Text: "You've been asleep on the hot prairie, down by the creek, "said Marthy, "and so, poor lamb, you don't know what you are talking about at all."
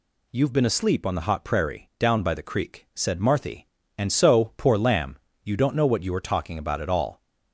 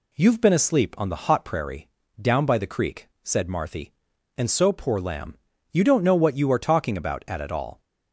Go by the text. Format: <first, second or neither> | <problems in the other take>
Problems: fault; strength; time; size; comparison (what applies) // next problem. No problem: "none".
first | says "at" twice; at 7.3 s